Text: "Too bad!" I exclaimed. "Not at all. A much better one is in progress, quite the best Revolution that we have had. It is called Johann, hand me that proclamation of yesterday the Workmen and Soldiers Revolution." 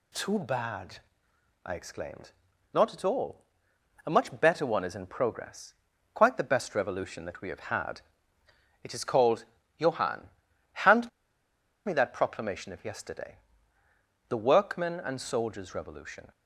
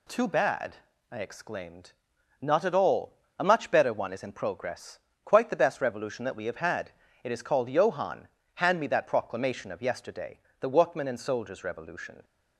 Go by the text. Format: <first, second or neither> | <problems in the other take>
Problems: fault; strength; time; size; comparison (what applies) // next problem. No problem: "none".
second | pauses between "called" and "Johann"; slight; at 9.4 s; 0.34 s long // pauses between "hand" and "me"; noticeable; at 11.0 s; 0.76 s long // pauses between "yesterday" and "the"; noticeable; at 13.3 s; 0.92 s long; slight in the second